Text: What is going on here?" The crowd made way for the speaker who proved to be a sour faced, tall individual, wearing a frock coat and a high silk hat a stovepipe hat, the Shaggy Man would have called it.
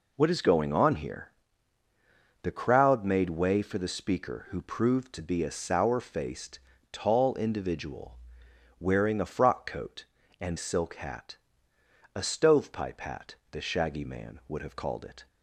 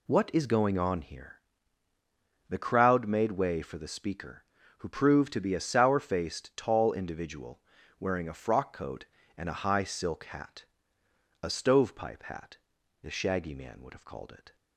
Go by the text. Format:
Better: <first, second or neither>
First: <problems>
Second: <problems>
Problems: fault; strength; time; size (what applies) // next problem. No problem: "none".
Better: second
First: skips "a high"; at 10.5 s // pauses between "hat" and "a"; noticeable; at 11.3 s; 0.78 s long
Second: pauses between "hat" and "a"; noticeable; at 10.6 s; 0.76 s long